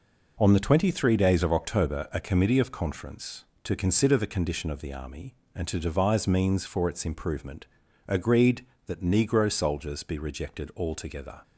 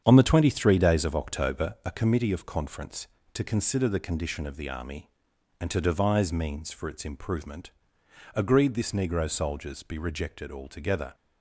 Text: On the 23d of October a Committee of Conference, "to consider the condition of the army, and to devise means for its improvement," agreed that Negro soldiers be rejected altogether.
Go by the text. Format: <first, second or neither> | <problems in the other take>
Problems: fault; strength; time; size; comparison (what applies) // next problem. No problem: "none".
first | starts louder than the rest; strong; until 1.0 s; 8 dB // says "this" for "that"; at 8.7 s